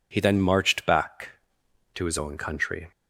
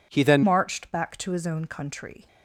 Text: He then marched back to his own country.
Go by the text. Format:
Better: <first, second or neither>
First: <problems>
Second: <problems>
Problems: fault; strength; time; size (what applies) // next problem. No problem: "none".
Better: first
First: none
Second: changes voice at "marched"; from 0.4 s on; 1.8 s long